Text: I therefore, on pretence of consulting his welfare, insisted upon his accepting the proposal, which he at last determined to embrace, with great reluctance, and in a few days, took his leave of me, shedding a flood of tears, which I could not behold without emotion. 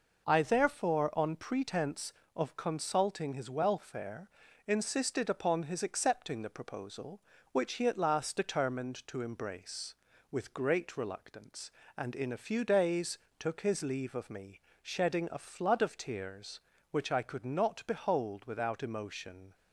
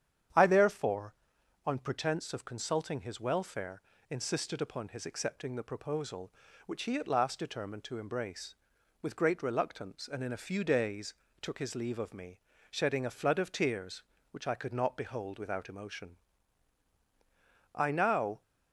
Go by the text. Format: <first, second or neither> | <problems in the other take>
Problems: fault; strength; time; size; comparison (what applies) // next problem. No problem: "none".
first | starts louder than the rest; strong; until 1.8 s; 9 dB // goes on to say "I now"; noticeable; from 17.7 s on; 0.66 s long